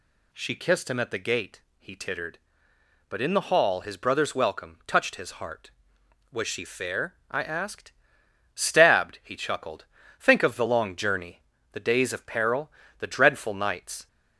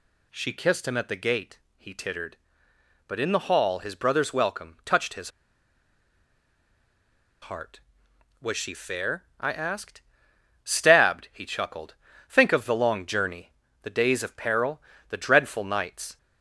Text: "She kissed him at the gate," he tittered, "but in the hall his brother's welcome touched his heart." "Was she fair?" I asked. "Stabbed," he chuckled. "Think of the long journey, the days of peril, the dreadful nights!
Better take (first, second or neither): first